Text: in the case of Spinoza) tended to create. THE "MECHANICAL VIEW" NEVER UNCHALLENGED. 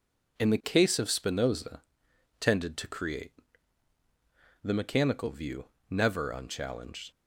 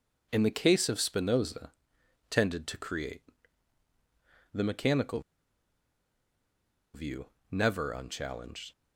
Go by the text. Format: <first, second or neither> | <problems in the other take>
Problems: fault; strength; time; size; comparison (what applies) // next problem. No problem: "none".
first | pauses between "MECHANICAL" and "VIEW"; strong; at 5.2 s; 1.7 s long // pauses between "VIEW" and "NEVER"; slight; at 7.2 s; 0.26 s long; slight in the first